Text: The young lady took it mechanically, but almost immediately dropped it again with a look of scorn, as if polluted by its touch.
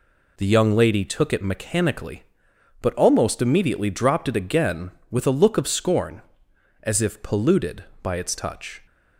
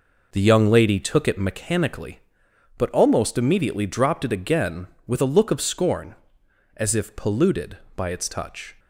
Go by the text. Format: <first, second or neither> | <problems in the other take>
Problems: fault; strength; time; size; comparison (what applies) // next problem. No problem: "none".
first | starts louder than the rest; noticeable; until 1.7 s; 5 dB